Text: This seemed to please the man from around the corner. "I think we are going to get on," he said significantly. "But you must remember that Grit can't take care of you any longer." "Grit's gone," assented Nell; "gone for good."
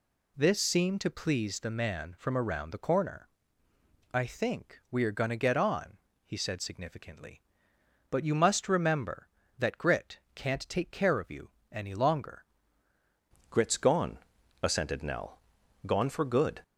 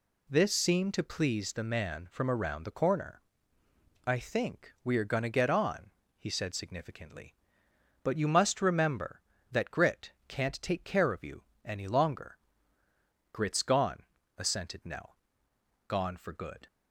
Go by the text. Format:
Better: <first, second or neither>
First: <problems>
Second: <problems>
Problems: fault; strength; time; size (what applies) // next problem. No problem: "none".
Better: second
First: pauses between "Grit" and "can't"; slight; at 10.1 s; 0.16 s long // pauses between "you" and "any"; slight; at 11.5 s; 0.20 s long // changes voice at "Grit's"; from 13.5 s on; 3.1 s long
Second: pauses between "Grit" and "can't"; slight; at 10.1 s; 0.16 s long // pauses between "you" and "any"; slight; at 11.4 s; 0.20 s long